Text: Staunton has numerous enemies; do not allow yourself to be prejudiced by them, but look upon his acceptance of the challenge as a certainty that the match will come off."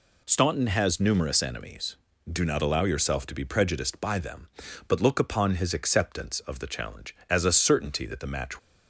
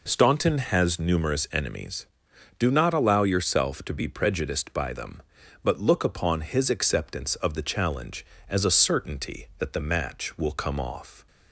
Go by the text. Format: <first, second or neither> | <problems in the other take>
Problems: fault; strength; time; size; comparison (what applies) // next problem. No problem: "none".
second | stops before "will come off"; at 8.5 s